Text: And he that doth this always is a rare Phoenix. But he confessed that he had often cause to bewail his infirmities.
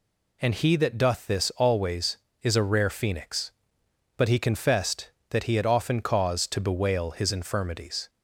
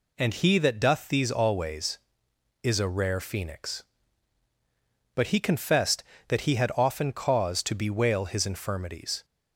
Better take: first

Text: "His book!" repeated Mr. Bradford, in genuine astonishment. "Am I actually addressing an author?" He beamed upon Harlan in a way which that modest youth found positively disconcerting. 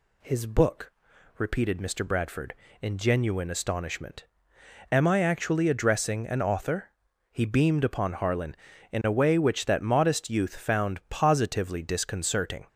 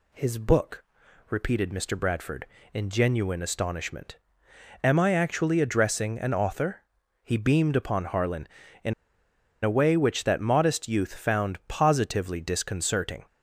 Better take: first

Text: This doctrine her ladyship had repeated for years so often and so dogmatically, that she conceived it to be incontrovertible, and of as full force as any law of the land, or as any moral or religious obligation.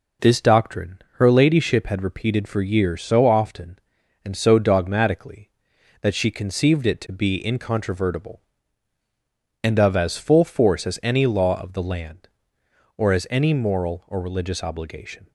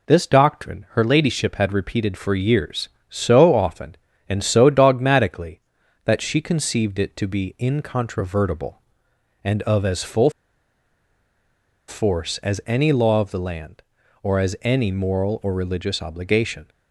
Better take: first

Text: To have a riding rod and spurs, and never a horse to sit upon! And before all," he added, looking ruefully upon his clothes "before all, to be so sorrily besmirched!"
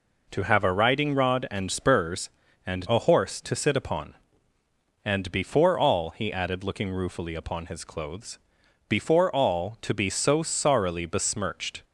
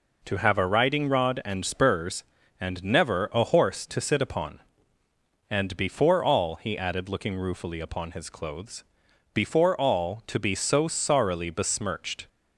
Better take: second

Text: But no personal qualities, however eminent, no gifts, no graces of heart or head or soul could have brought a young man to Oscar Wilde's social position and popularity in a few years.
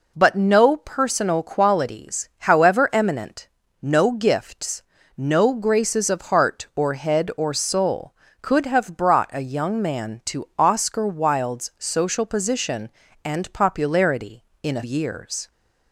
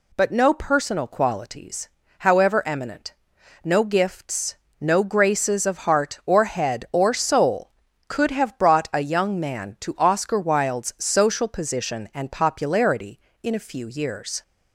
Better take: second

